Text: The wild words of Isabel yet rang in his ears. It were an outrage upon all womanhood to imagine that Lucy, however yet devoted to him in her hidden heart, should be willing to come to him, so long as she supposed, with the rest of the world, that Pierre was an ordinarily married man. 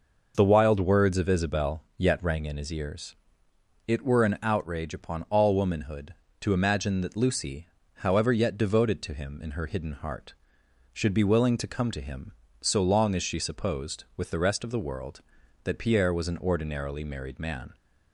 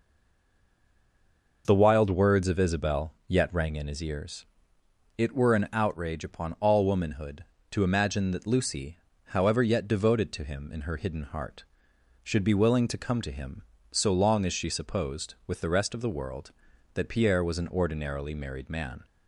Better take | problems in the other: first | stays silent before the first word; noticeable; until 1.6 s; 1.6 s long

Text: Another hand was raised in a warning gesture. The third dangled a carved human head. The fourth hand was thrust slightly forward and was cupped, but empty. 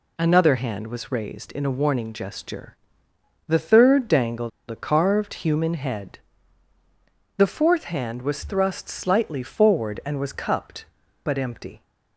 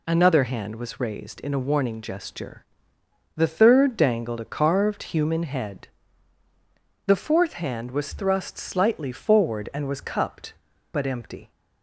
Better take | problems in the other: second | pauses between "dangled" and "a"; slight; at 4.5 s; 0.20 s long

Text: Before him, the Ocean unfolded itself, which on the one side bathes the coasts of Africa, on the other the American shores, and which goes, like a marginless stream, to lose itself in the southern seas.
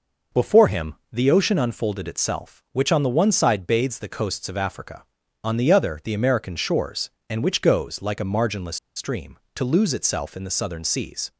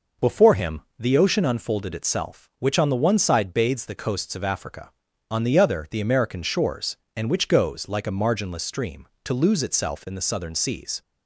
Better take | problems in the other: second | pauses between "marginless" and "stream"; slight; at 8.7 s; 0.19 s long

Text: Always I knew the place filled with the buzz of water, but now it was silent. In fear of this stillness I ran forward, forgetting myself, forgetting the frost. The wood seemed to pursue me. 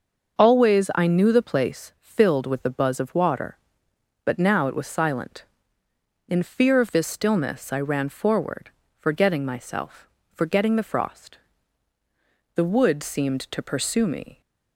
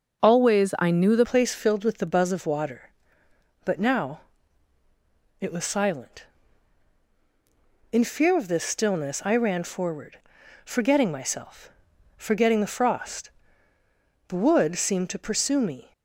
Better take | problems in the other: first | starts louder than the rest; until 1.2 s; 6.5 dB; also in the first // changes voice at "place"; from 1.2 s on; 14.7 s long // pauses between "now" and "it"; at 4.2 s; 1.1 s long

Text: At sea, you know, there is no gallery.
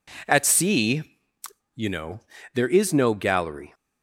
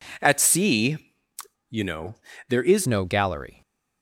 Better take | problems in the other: first | changes voice at "no"; from 2.8 s on; 0.8 s long

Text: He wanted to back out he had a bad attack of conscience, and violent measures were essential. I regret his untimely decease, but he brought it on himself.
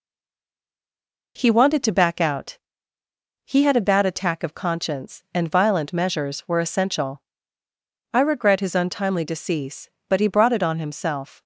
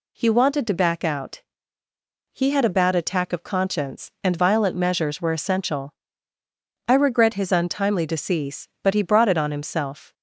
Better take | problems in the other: second | stays silent before the first word; noticeable; until 1.3 s; 1.3 s long // pauses between "out" and "he"; noticeable; at 2.5 s; 0.88 s long; noticeable in the second

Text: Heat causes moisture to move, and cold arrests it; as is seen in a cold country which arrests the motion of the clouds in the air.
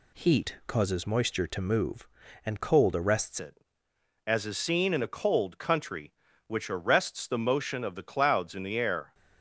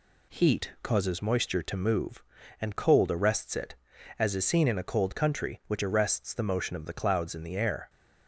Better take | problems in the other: second | changes voice at "it"; from 3.3 s on; 5.8 s long

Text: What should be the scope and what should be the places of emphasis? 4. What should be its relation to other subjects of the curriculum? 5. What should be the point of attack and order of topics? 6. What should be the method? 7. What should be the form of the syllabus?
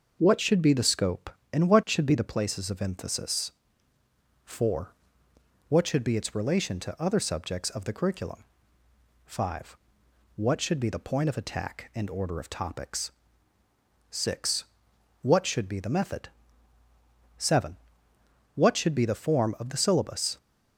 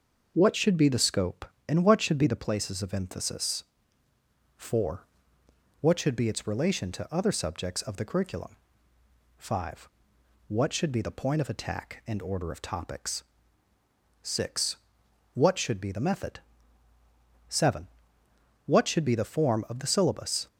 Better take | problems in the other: neither | starts louder than the rest; noticeable; the same in both

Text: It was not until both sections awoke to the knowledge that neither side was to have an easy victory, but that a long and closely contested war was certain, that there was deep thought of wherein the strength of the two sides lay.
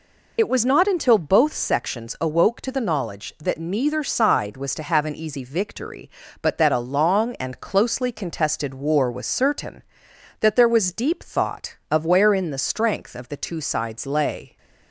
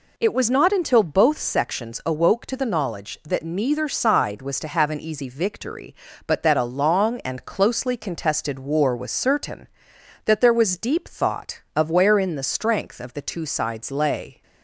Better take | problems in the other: second | loses the start of "It"; at 0.3 s; 55 ms

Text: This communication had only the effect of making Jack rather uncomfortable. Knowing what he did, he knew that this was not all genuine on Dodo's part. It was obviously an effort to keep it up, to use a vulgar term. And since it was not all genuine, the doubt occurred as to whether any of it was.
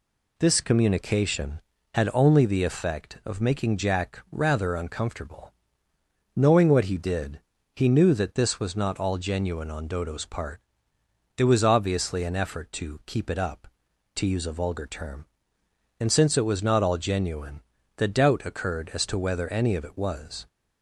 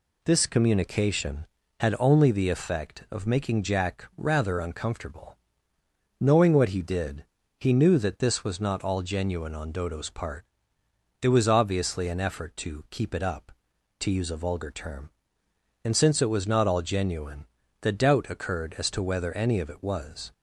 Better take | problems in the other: neither | none

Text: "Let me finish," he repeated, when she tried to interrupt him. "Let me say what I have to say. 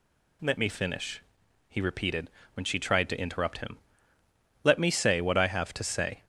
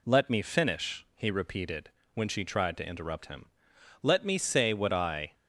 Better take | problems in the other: first | stops before "have to say"; at 5.3 s

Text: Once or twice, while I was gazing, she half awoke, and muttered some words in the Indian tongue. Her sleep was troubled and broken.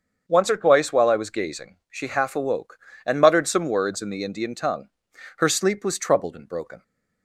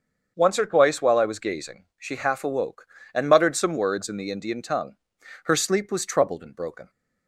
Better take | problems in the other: neither | starts louder than the rest; the same in both

